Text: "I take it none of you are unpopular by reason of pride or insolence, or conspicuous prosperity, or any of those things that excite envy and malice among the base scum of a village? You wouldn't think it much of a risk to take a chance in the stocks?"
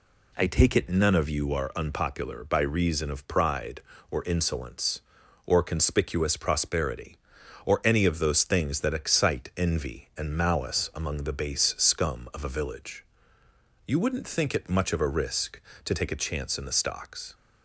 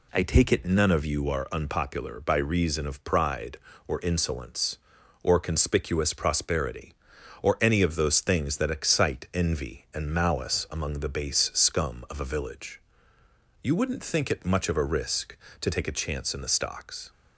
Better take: neither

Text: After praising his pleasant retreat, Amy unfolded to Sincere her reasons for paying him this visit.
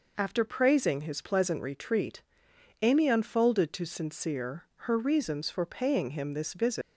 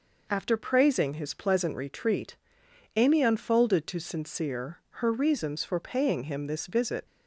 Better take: second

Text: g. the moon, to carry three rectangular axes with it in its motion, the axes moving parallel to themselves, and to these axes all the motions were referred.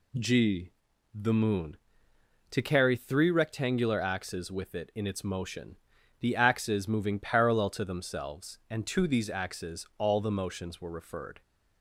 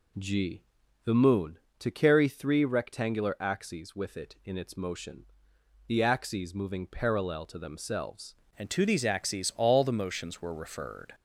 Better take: first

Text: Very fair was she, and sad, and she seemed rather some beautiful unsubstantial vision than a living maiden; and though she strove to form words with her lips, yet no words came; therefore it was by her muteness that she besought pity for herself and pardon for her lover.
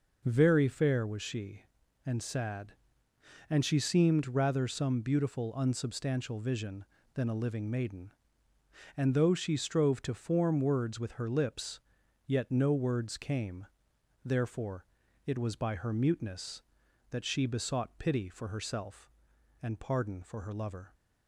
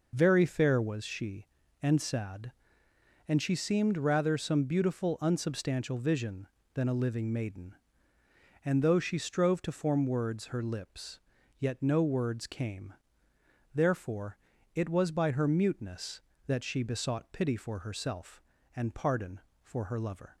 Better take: first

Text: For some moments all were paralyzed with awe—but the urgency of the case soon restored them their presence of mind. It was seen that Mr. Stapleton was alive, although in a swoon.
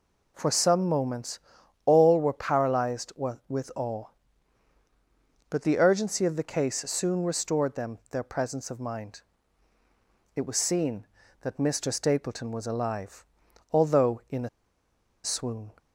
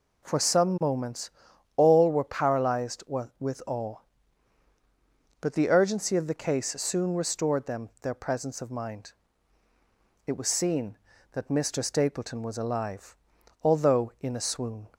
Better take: second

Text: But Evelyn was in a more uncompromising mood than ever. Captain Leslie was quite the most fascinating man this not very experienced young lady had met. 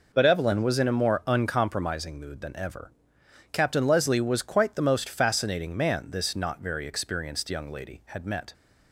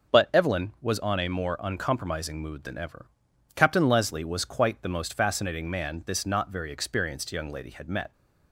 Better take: first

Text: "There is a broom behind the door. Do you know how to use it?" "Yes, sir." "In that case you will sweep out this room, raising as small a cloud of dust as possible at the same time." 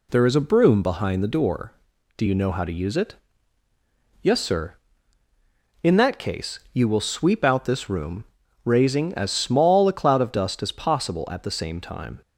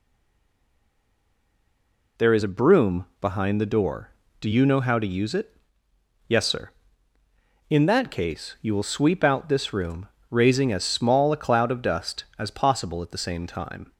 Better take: first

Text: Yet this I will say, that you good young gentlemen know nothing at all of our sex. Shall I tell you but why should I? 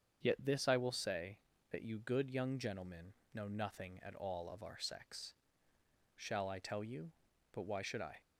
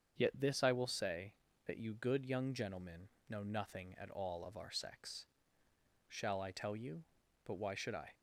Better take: neither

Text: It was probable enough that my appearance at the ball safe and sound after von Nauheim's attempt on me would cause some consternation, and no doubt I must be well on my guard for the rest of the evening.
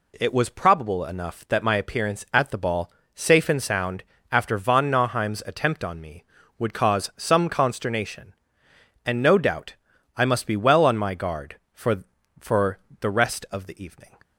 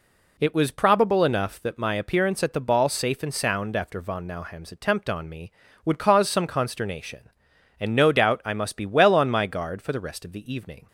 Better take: second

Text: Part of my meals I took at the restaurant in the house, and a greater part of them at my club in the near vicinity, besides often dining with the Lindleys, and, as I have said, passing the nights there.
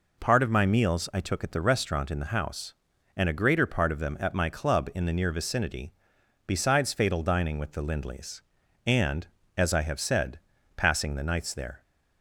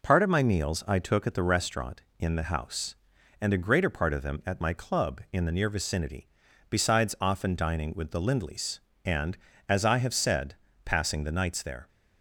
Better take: second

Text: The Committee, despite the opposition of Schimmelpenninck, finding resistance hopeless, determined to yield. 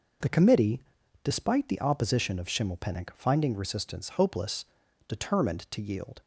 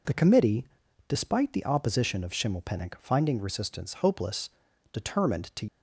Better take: first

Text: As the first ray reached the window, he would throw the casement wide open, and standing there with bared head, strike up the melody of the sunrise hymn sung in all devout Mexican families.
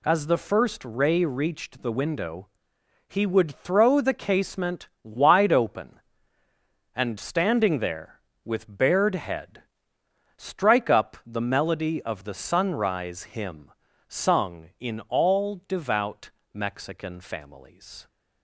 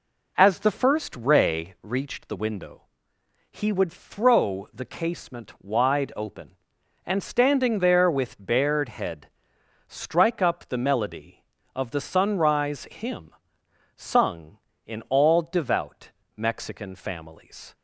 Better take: first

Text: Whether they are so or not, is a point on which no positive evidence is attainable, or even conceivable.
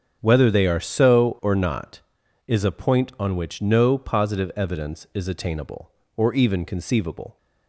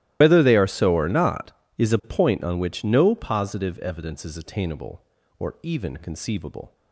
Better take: first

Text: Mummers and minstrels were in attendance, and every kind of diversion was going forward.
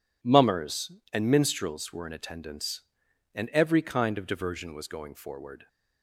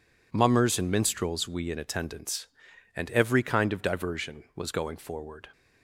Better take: first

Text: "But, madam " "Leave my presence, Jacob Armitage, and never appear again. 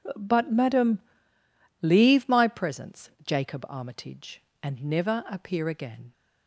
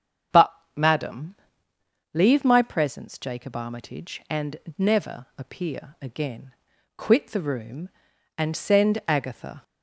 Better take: first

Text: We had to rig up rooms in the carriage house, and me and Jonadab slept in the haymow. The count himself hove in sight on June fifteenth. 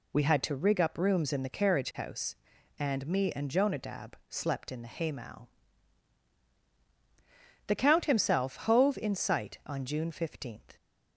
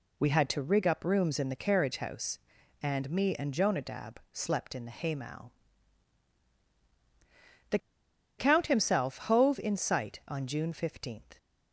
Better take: first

